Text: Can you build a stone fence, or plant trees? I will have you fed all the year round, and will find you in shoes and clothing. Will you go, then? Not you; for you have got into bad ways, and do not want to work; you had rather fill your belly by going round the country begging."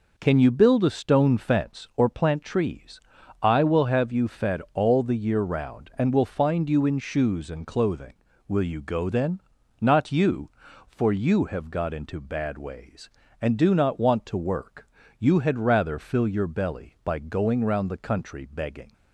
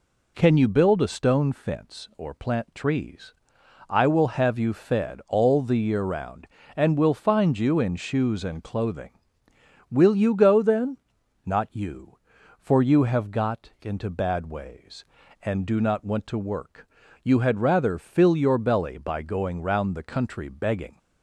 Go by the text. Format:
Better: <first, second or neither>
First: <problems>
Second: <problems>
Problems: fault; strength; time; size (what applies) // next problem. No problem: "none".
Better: neither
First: none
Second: none